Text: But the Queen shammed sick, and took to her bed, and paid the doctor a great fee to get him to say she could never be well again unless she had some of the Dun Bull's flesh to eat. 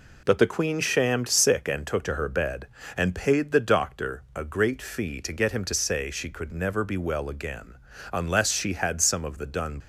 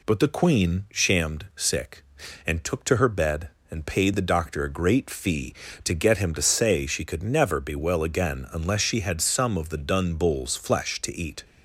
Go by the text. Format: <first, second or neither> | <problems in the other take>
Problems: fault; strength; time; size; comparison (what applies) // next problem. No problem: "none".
second | pauses between "again" and "unless"; slight; at 7.7 s; 0.34 s long // stops before "Bull's flesh to eat"; at 9.7 s